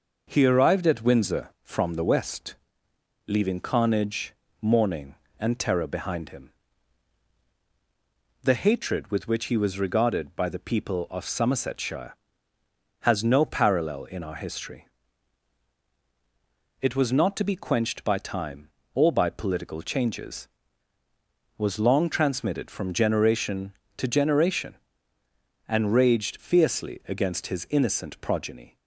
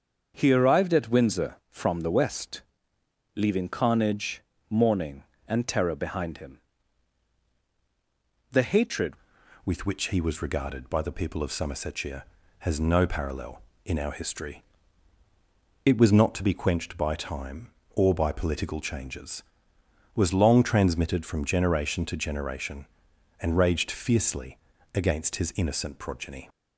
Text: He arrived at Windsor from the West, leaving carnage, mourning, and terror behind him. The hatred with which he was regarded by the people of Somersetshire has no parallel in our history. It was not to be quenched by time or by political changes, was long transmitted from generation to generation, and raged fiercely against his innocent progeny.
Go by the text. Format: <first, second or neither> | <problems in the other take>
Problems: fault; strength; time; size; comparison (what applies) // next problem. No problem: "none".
first | starts louder than the rest; until 1.3 s; 7 dB // changes voice at "with"; from 9.6 s on; 16.8 s long // pauses between "fiercely" and "against"; at 24.5 s; 0.38 s long